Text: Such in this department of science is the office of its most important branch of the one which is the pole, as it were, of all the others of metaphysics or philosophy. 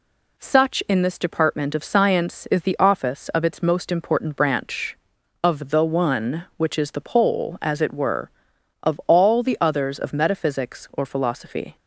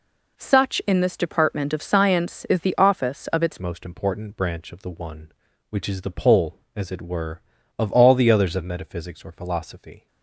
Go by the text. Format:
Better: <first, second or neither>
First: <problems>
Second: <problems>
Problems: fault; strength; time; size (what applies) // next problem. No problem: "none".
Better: first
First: none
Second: changes voice at "most"; from 3.6 s on; 6.4 s long